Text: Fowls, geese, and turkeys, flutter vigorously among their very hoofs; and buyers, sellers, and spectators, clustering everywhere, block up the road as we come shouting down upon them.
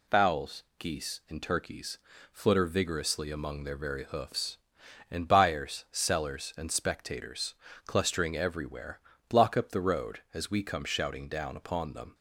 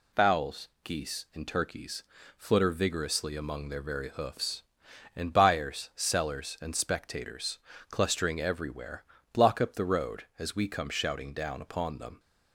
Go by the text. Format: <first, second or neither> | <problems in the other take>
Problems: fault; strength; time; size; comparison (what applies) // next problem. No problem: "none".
neither | none